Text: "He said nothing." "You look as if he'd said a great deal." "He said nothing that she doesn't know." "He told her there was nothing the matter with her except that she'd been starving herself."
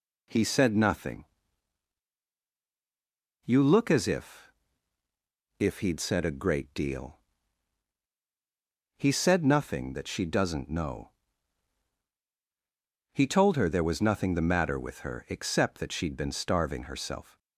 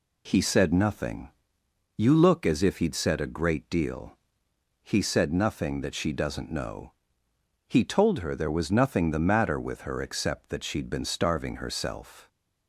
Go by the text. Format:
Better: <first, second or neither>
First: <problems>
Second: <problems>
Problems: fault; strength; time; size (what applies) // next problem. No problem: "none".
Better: second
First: says "if" twice; at 5.5 s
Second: none